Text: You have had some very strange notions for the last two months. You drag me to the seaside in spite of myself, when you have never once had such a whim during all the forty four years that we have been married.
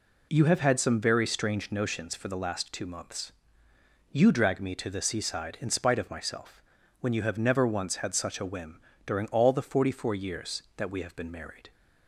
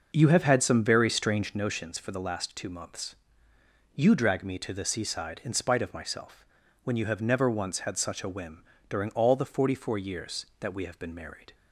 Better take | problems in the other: first | starts louder than the rest; noticeable; until 1.7 s; 6 dB // pauses between "whim" and "during"; slight; at 8.6 s; 0.28 s long; slight in the first

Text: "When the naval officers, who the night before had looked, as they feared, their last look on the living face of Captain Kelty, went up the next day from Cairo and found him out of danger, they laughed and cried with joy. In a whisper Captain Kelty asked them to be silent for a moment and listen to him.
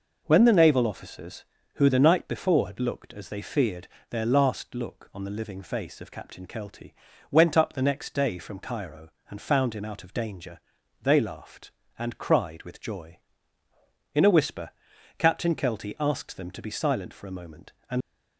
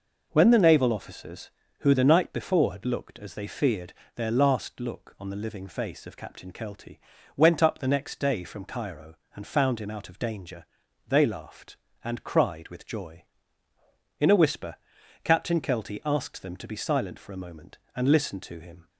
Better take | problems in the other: second | pauses between "whisper" and "Captain"; noticeable; at 14.7 s; 0.46 s long; noticeable in the second // stops before "listen to him"; at 18.0 s

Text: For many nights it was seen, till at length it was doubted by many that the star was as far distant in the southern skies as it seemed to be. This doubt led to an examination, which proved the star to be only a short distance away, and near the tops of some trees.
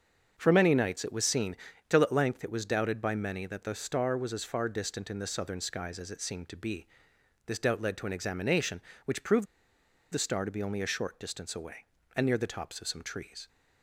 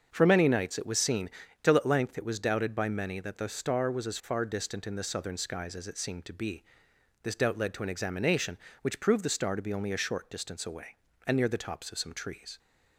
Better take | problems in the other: second | starts louder than the rest; until 1.3 s; 6.5 dB; also in the second // pauses between "proved" and "the"; noticeable; at 9.4 s; 0.67 s long

